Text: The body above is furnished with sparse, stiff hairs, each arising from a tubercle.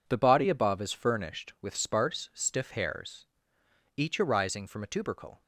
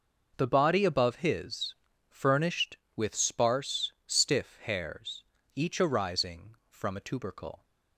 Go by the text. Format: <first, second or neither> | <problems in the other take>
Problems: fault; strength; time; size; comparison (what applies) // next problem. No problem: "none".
first | says "his" for "is"; at 1.1 s